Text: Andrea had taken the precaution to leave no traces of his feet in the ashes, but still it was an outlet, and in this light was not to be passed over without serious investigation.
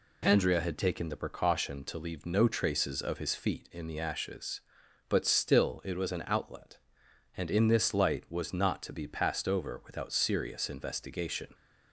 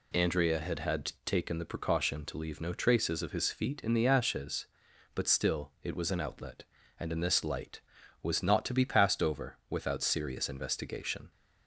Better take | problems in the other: first | says "had" twice; at 0.8 s

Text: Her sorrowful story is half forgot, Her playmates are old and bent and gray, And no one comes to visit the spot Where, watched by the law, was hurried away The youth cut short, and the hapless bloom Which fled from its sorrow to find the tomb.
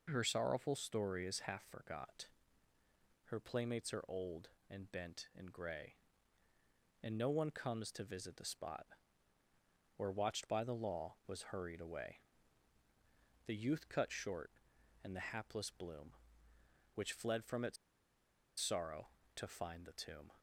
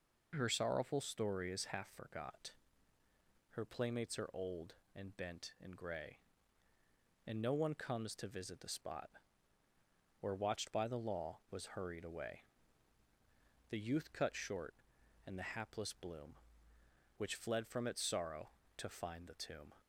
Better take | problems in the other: second | pauses between "spot" and "Where"; at 8.8 s; 1.1 s long; also in the second // pauses between "away" and "The"; at 12.2 s; 1.2 s long; also in the second // pauses between "its" and "sorrow"; noticeable; at 17.7 s; 0.83 s long

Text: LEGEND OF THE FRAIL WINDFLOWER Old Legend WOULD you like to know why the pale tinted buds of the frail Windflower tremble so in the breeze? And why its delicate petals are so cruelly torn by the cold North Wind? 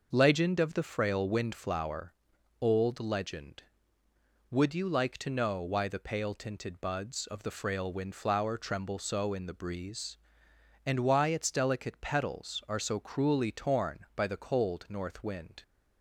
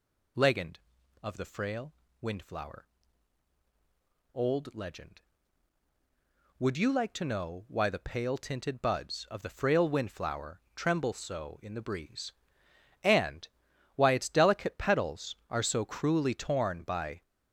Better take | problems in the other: first | pauses between "FRAIL" and "WINDFLOWER"; slight; at 1.9 s; 0.28 s long // pauses between "WINDFLOWER" and "Old"; strong; at 2.8 s; 1.4 s long; noticeable in the first // pauses between "Windflower" and "tremble"; slight; at 10.6 s; 0.16 s long // pauses between "And" and "why"; noticeable; at 13.4 s; 0.48 s long // stops before "the cold North Wind"; at 17.2 s

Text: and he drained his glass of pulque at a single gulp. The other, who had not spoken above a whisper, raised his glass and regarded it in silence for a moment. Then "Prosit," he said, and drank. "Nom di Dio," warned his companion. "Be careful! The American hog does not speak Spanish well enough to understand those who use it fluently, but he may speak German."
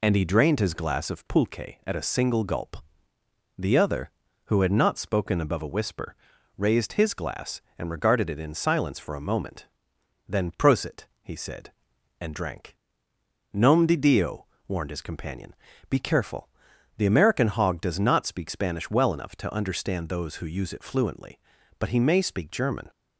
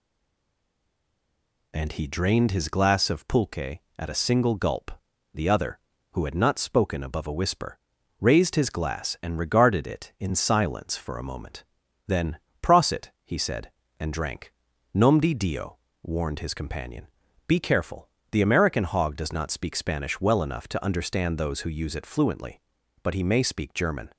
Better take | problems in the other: first | stays silent before the first word; noticeable; until 1.7 s; 1.7 s long // pauses between "Then" and "Prosit"; slight; at 12.3 s; 0.24 s long

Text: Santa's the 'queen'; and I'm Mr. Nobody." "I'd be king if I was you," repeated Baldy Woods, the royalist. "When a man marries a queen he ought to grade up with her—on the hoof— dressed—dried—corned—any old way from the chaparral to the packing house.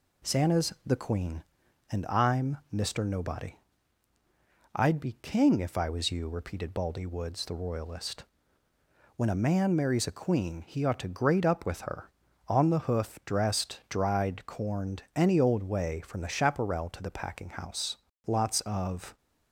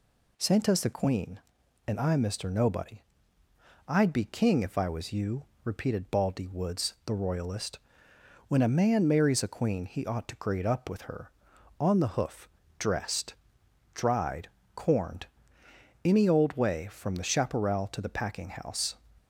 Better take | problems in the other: second | goes on to say "Lots of"; noticeable; from 18.2 s on; 0.92 s long

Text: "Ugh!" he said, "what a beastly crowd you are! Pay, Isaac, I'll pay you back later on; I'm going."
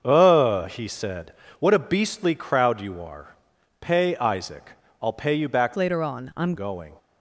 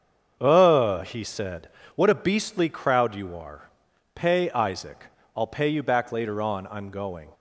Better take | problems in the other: second | starts louder than the rest; until 1.0 s; 6.5 dB; also in the second // changes voice from "later" to "I'm"; from 5.7 to 6.5 s; 0.8 s long

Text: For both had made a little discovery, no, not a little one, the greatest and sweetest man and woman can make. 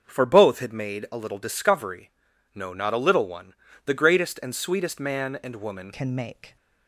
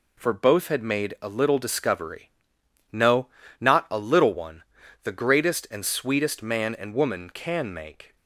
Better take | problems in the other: second | starts louder than the rest; until 1.0 s; 6.5 dB // changes voice at "can"; from 5.9 s on; 0.6 s long

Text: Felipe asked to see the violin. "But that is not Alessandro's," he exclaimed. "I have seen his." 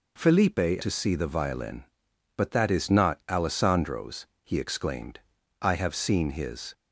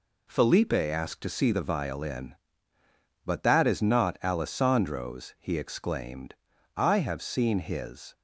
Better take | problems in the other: second | skips "asked"; at 0.8 s

